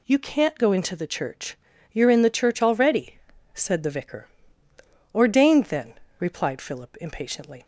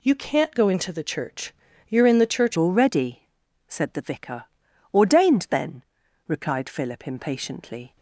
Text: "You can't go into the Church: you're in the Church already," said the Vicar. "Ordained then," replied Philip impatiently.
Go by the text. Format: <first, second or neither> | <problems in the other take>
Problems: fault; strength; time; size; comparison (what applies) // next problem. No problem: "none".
first | changes voice at "already"; from 2.5 s on; 5.4 s long